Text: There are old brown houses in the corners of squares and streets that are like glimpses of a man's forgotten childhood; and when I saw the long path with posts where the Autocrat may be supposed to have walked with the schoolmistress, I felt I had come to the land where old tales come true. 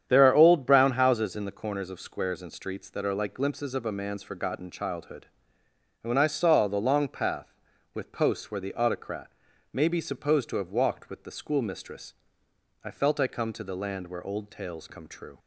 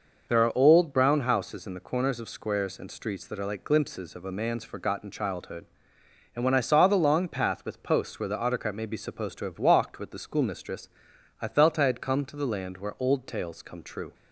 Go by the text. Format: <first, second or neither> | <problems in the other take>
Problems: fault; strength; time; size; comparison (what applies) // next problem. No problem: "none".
second | starts louder than the rest; strong; until 1.0 s; 9 dB // pauses between "Autocrat" and "may"; at 9.3 s; 0.40 s long // skips "had"; at 13.2 s